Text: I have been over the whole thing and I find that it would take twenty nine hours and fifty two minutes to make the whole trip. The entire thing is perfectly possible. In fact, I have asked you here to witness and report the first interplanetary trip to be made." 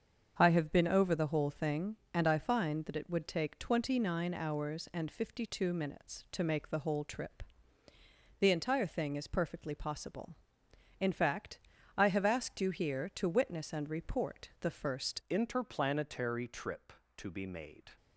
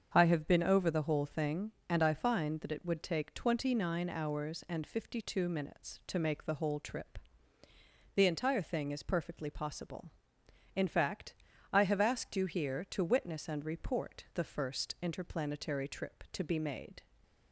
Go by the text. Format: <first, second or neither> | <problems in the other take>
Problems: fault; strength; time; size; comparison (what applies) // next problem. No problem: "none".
second | starts louder than the rest; until 1.3 s; 7 dB; also in the second // changes voice at "interplanetary"; from 15.2 s on; 2.7 s long